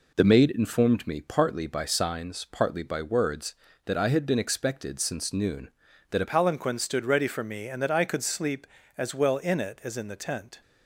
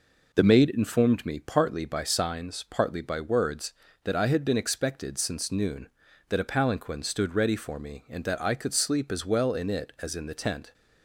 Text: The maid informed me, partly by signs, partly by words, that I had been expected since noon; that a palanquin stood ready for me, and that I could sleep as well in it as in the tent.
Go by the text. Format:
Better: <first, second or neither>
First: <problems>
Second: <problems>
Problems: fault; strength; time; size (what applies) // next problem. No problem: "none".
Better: second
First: changes voice at "palanquin"; from 6.2 s on; 4.4 s long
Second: none